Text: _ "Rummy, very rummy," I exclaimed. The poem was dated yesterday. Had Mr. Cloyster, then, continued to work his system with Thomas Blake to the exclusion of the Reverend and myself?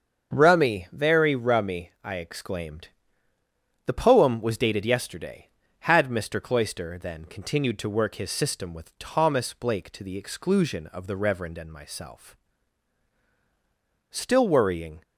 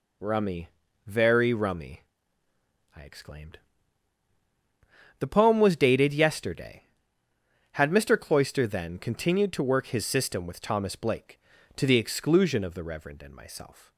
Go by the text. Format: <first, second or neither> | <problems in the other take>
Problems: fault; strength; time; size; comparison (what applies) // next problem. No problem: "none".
second | starts louder than the rest; until 1.3 s; 7 dB // goes on to say "Still worrying"; noticeable; from 14.0 s on; 0.92 s long